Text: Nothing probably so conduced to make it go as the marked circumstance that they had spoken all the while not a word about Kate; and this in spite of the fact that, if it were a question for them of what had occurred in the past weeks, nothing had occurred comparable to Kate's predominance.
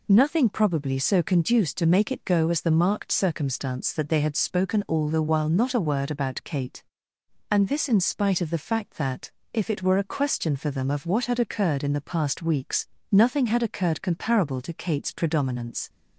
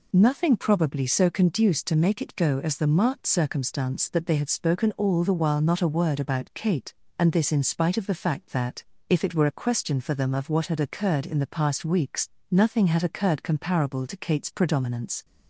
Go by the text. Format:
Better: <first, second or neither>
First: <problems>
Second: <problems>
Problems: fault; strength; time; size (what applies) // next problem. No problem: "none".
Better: neither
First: none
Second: none